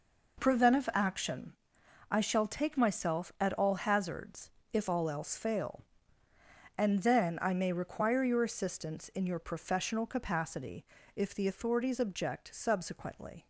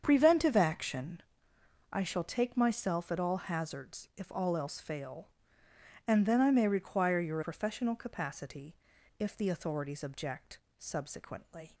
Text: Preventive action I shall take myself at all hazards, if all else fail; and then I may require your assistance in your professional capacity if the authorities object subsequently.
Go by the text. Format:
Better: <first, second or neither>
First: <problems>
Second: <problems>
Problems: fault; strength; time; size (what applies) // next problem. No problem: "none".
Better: first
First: pauses between "action" and "I"; noticeable; at 1.5 s; 0.58 s long // pauses between "capacity" and "if"; slight; at 10.8 s; 0.32 s long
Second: starts louder than the rest; strong; until 1.0 s; 7.5 dB // pauses between "action" and "I"; noticeable; at 1.2 s; 0.68 s long // skips "assistance in your"; at 7.4 s // pauses between "capacity" and "if"; at 8.7 s; 0.42 s long // pauses between "object" and "subsequently"; slight; at 10.6 s; 0.18 s long